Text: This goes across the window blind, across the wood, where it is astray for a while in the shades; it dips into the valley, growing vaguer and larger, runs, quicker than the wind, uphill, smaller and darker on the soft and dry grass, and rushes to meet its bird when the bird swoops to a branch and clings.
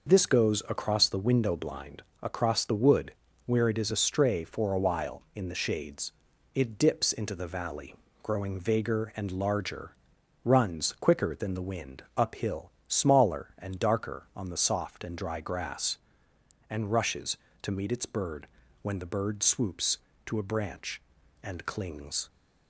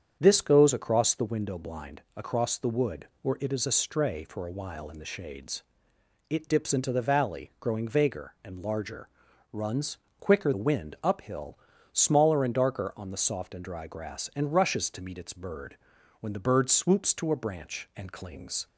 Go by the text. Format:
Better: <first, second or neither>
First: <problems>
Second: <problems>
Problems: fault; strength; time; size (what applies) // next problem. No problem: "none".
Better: first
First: pauses between "bird" and "when"; slight; at 18.4 s; 0.36 s long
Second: starts louder than the rest; strong; until 1.2 s; 8 dB // skips "than"; at 10.5 s // pauses between "bird" and "when"; at 15.7 s; 0.42 s long